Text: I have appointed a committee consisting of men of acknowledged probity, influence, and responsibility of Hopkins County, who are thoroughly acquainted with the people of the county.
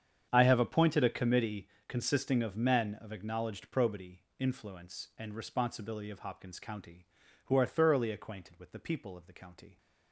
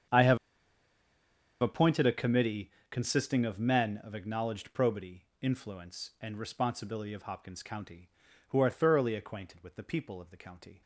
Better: first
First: starts louder than the rest; strong; until 1.3 s; 8 dB // pauses between "committee" and "consisting"; slight; at 1.6 s; 0.18 s long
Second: starts louder than the rest; strong; until 2.3 s; 8 dB // pauses between "have" and "appointed"; at 0.3 s; 1.2 s long // pauses between "committee" and "consisting"; slight; at 2.7 s; 0.18 s long

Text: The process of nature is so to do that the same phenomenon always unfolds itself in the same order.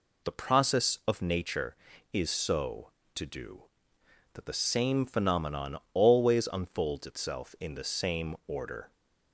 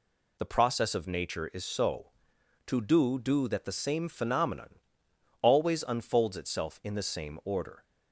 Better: first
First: pauses between "phenomenon" and "always"; slight; at 5.7 s; 0.16 s long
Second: says "do" twice; at 3.1 s // pauses between "phenomenon" and "always"; noticeable; at 4.7 s; 0.62 s long

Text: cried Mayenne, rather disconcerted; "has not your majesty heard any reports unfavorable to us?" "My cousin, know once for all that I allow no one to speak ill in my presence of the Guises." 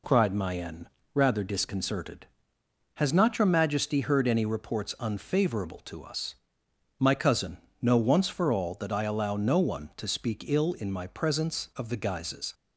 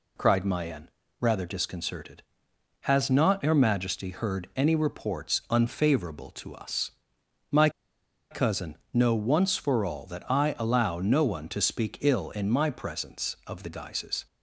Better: first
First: none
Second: pauses between "My" and "cousin"; noticeable; at 7.6 s; 0.61 s long

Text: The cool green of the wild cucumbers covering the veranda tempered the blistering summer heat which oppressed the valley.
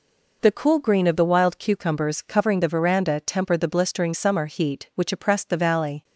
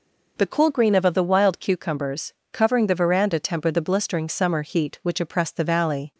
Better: first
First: none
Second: says "of" twice; at 1.0 s // pauses between "cucumbers" and "covering"; slight; at 2.3 s; 0.17 s long

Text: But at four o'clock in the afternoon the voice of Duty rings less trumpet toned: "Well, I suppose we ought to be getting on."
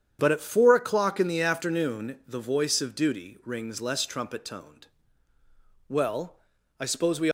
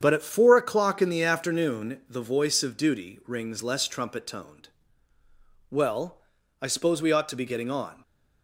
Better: second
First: starts louder than the rest; strong; until 1.2 s; 8.5 dB // stops before "ought to be getting on"; at 7.2 s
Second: starts louder than the rest; strong; until 1.0 s; 8 dB

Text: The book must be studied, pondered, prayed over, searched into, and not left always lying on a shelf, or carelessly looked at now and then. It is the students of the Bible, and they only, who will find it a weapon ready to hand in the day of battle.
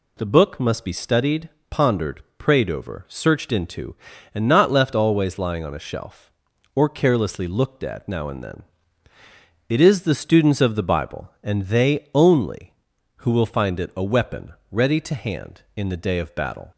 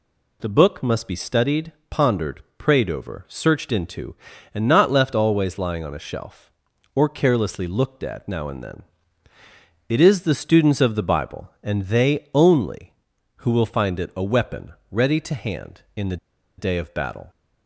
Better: first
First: pauses between "weapon" and "ready"; slight; at 14.5 s; 0.18 s long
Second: pauses between "weapon" and "ready"; slight; at 14.7 s; 0.18 s long // pauses between "the" and "day"; at 16.1 s; 0.41 s long

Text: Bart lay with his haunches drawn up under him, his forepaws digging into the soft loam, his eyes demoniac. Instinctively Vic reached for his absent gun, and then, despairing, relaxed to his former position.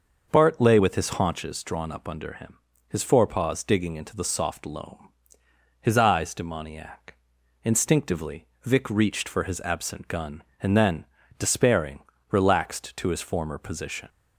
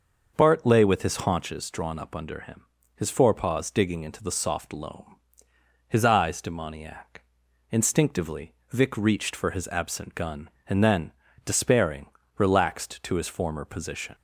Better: neither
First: starts louder than the rest; until 1.3 s; 6 dB // pauses between "Instinctively" and "Vic"; slight; at 8.4 s; 0.18 s long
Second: starts louder than the rest; until 1.3 s; 6 dB // pauses between "Instinctively" and "Vic"; slight; at 8.5 s; 0.18 s long

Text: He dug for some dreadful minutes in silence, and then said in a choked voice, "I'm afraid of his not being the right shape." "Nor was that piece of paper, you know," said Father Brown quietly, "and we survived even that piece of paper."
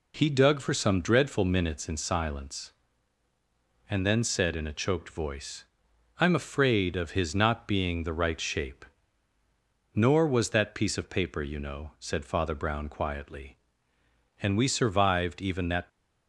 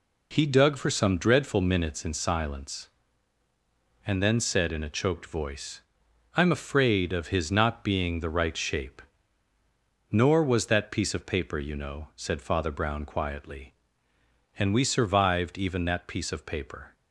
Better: second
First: stops before "piece of paper"; at 15.8 s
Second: none

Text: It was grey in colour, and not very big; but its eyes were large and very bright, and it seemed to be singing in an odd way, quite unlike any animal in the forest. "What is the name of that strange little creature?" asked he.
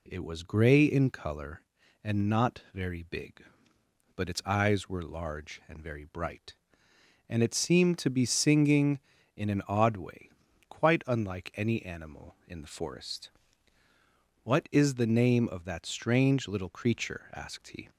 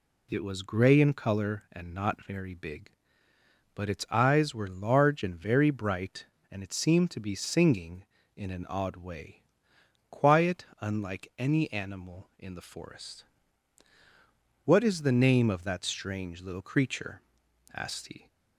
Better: first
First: none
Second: says "quiet" for "quite"; at 10.1 s

